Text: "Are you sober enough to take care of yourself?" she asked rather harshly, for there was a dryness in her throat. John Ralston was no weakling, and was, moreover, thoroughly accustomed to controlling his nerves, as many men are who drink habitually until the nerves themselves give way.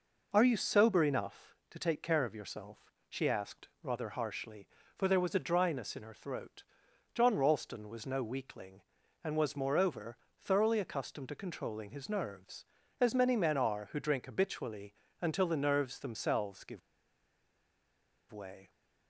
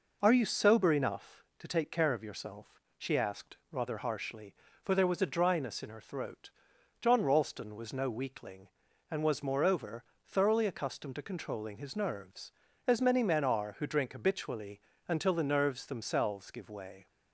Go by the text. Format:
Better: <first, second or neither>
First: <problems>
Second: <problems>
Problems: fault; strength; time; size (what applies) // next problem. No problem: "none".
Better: second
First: pauses between "habitually" and "until"; slight; at 14.9 s; 0.28 s long // pauses between "give" and "way"; strong; at 16.8 s; 1.5 s long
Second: pauses between "habitually" and "until"; slight; at 14.7 s; 0.28 s long